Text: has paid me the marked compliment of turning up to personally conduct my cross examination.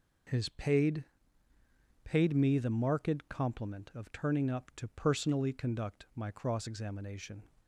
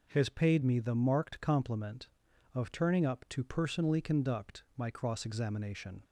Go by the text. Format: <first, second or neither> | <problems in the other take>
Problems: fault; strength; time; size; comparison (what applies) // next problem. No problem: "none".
second | says "paid" twice; at 2.0 s